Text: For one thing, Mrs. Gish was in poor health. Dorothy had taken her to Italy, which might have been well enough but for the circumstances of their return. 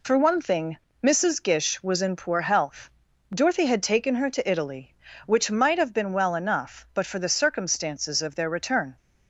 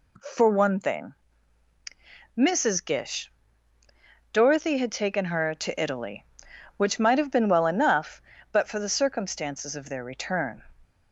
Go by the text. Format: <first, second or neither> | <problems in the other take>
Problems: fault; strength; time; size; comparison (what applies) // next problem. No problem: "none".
first | skips "was in poor health"; at 3.8 s